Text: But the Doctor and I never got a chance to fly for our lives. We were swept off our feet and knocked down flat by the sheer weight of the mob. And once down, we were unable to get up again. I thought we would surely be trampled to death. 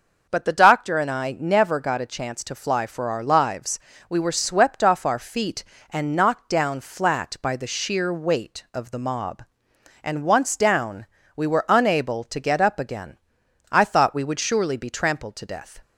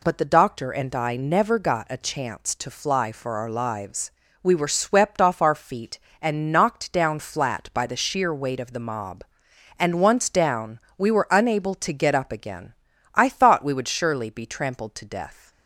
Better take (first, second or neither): neither